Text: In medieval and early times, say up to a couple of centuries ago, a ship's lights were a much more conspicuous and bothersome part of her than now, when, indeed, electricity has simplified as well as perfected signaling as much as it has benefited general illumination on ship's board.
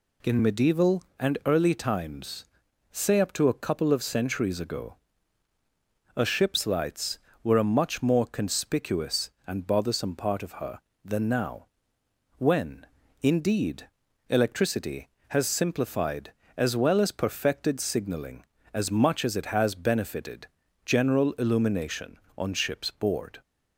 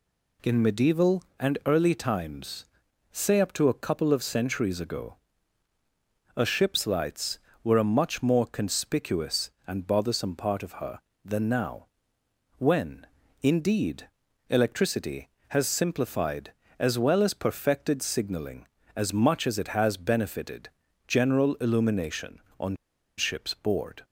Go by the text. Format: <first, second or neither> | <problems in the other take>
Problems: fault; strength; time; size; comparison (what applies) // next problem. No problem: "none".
first | pauses between "benefited" and "general"; slight; at 20.6 s; 0.36 s long; slight in the first // pauses between "on" and "ship's"; at 22.7 s; 0.41 s long